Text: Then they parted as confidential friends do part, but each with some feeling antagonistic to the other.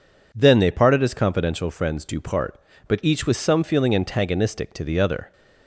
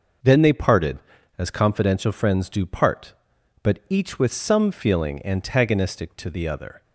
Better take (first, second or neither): neither